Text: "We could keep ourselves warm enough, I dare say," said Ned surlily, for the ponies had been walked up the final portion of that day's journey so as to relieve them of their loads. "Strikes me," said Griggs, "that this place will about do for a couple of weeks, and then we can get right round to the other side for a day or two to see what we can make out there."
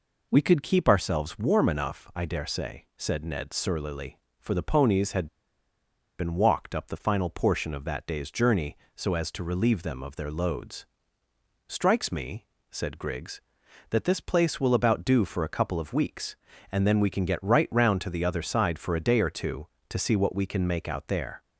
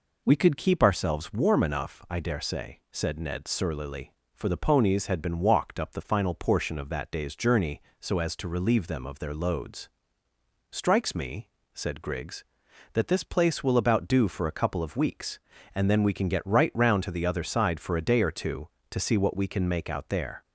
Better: second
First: pauses between "had" and "been"; noticeable; at 5.2 s; 0.92 s long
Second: none

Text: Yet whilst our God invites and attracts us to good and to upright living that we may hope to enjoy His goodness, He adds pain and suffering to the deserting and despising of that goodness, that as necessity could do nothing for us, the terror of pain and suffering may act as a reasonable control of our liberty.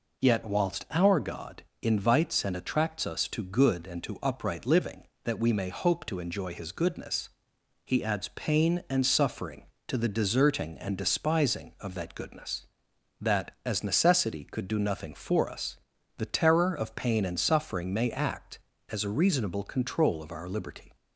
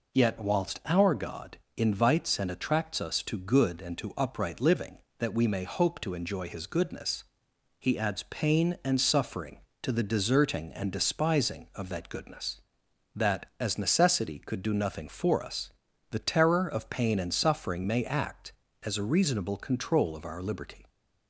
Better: neither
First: pauses between "God" and "invites"; slight; at 1.6 s; 0.20 s long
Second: pauses between "God" and "invites"; slight; at 1.5 s; 0.20 s long

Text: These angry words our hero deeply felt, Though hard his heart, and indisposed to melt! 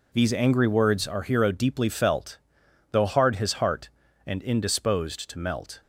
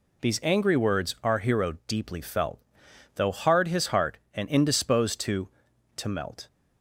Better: first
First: none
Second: says "to" twice; at 5.9 s

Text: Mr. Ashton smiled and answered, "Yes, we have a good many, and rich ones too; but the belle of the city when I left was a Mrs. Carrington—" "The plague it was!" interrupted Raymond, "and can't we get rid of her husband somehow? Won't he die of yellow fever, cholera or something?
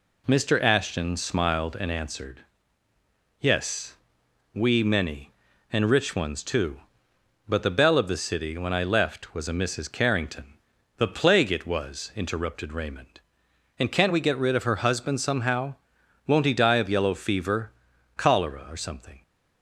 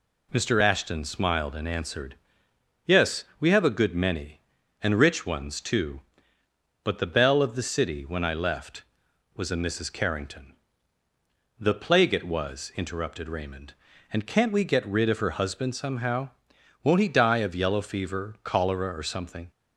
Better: second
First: skips "have a good"; at 4.8 s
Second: none

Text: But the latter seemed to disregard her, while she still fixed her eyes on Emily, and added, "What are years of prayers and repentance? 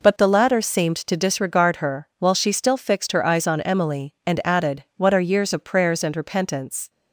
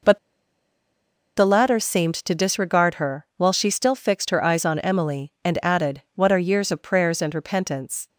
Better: first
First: none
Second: pauses between "But" and "the"; at 0.1 s; 1.1 s long

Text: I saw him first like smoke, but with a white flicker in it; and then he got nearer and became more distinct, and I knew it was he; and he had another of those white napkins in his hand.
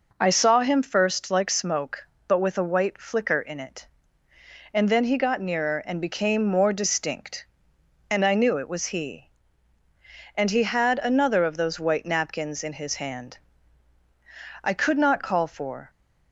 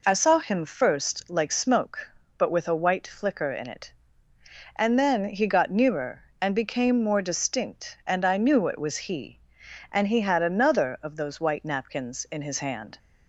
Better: second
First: goes on to say "I could not call for"; noticeable; from 14.6 s on; 1.2 s long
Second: none

